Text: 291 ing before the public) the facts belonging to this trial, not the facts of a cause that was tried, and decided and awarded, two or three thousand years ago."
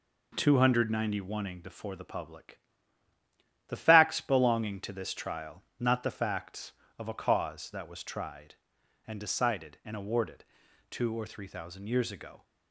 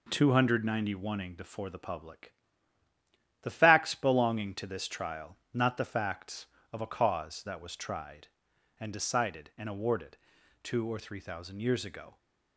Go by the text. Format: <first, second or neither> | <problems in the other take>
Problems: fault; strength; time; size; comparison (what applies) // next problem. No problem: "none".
neither | none